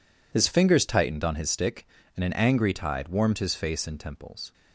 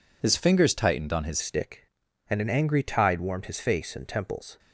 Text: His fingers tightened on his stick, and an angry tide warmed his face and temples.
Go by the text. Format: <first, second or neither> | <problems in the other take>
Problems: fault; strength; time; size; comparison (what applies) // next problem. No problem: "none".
first | changes voice at "stick"; from 1.4 s on; 3.1 s long